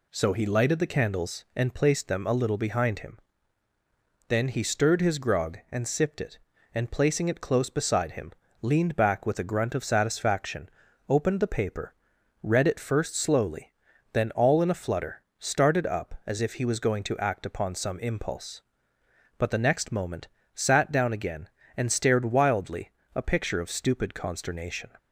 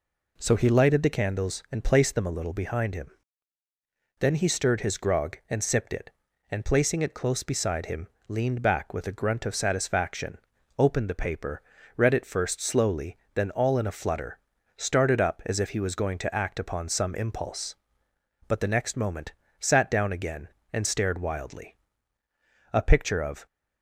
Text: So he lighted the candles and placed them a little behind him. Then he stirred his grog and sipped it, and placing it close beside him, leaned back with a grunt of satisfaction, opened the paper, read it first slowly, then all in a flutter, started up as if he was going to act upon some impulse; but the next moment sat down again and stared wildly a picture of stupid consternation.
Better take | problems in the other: first | pauses between "moment" and "sat"; slight; at 19.3 s; 0.26 s long; slight in the first // pauses between "wildly" and "a"; noticeable; at 21.7 s; 0.98 s long; slight in the first // stops before "stupid consternation"; at 23.4 s

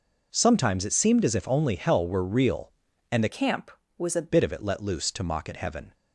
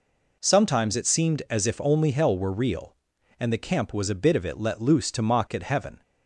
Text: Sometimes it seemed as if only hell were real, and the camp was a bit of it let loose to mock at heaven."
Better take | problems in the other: second | changes voice from "camp" to "a"; from 3.2 to 4.2 s; 1.0 s long

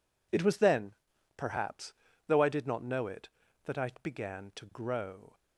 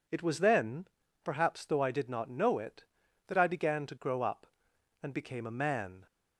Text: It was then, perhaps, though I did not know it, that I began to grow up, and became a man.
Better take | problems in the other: second | stops before "up and became a man"; at 5.3 s

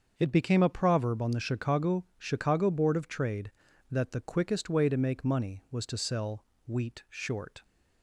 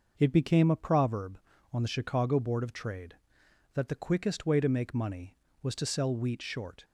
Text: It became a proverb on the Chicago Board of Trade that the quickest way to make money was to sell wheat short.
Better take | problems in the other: second | starts louder than the rest; until 1.1 s; 6.5 dB // says "Chicago" twice; at 2.1 s // pauses between "sell" and "wheat"; slight; at 6.4 s; 0.20 s long

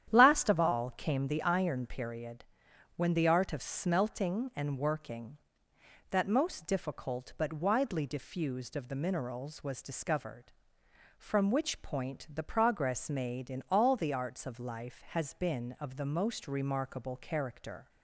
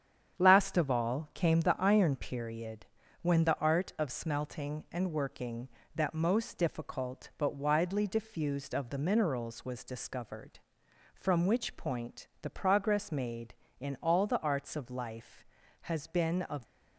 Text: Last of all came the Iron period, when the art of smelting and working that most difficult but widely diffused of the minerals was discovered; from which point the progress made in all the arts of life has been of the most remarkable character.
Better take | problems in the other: first | starts louder than the rest; strong; until 1.4 s; 8.5 dB; strong in the first // stops before "the most remarkable character"; at 16.6 s

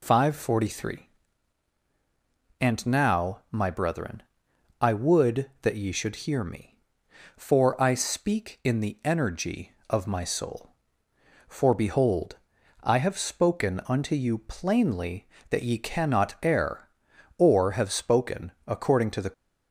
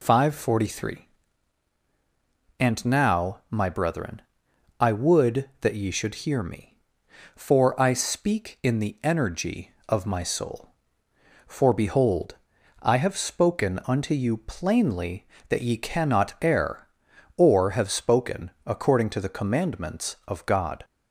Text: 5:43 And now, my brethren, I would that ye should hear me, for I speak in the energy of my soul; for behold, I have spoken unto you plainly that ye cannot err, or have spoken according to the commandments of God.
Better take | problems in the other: second | pauses between "spoken" and "according"; slight; at 18.5 s; 0.16 s long; slight in the second // stops before "commandments of God"; at 19.3 s

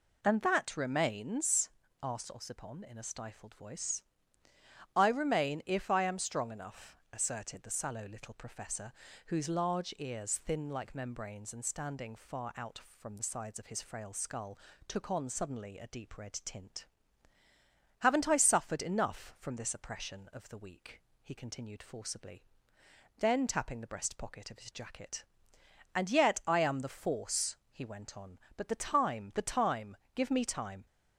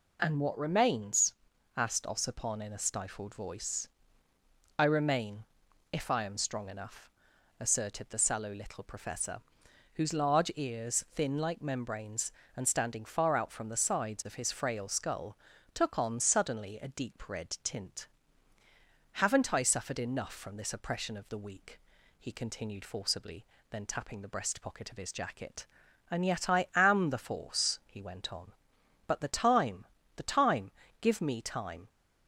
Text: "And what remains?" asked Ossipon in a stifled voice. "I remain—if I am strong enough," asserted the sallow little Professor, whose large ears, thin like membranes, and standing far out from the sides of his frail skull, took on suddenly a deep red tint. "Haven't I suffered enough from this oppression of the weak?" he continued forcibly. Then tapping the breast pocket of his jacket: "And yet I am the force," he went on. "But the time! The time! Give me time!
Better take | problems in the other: second | says "that" for "what"; at 0.4 s

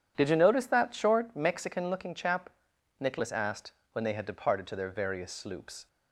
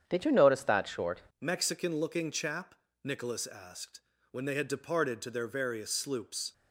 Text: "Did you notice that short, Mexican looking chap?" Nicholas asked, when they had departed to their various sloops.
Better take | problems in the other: first | starts louder than the rest; strong; until 1.1 s; 8.5 dB // changes voice at "Mexican"; from 1.4 s on; 5.1 s long

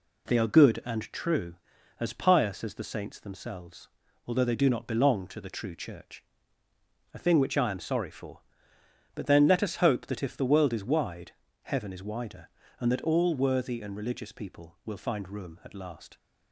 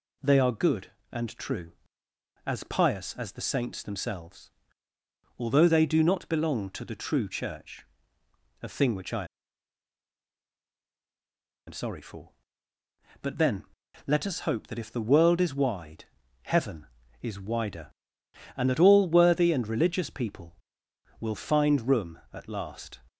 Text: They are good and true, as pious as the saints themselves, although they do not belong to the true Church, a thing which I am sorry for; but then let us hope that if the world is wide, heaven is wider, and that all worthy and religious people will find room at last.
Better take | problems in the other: first | pauses between "I" and "am"; strong; at 9.2 s; 2.4 s long // pauses between "then" and "let"; noticeable; at 13.6 s; 0.46 s long

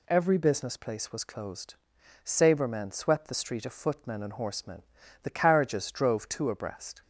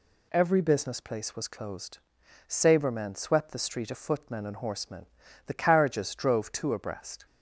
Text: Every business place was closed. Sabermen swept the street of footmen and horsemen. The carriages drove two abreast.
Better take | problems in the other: neither | none

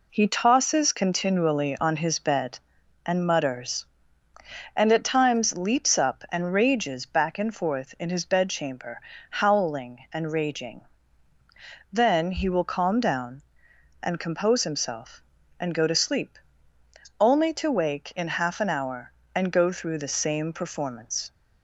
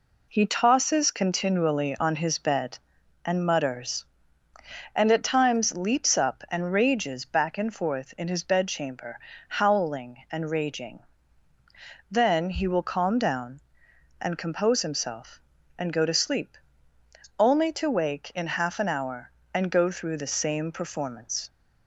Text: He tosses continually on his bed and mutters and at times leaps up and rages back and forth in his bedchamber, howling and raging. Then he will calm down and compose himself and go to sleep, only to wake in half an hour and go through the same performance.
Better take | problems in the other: neither | none

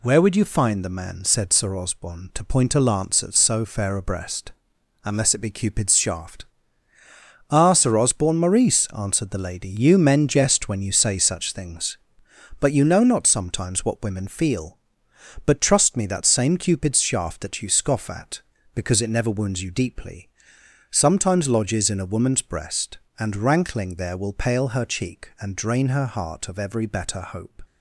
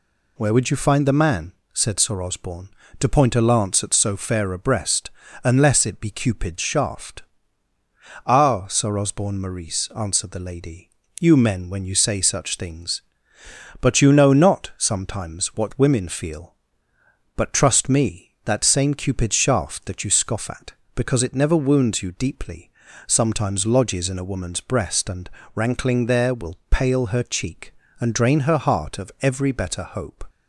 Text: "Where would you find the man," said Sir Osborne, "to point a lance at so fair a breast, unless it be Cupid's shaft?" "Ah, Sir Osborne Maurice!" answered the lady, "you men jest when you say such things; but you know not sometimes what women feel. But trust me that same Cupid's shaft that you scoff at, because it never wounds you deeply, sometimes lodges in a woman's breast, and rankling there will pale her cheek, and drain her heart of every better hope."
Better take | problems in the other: first | skips "jest"; at 11.6 s // pauses between "and" and "rankling"; slight; at 25.2 s; 0.24 s long

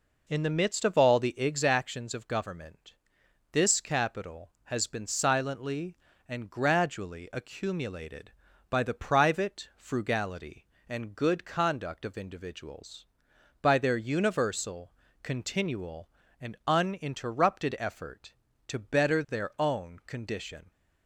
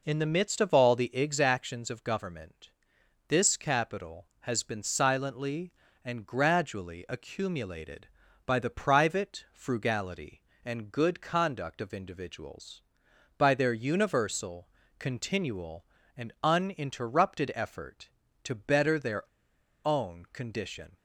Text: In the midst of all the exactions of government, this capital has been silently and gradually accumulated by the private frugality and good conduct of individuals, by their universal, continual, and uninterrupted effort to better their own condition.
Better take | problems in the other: first | pauses between "their" and "own"; noticeable; at 19.2 s; 0.61 s long

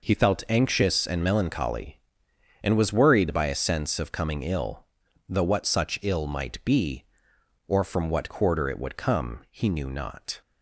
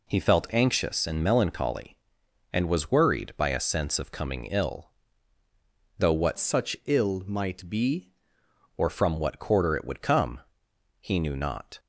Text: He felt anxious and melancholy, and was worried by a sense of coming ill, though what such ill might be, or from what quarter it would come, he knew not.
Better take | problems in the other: first | changes voice from "such" to "be"; from 6.3 to 8.1 s; 1.8 s long

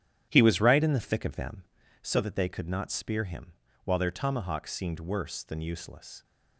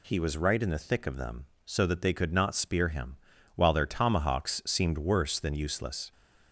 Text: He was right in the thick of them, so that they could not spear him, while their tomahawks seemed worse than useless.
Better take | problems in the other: second | starts louder than the rest; strong; until 2.1 s; 10.5 dB

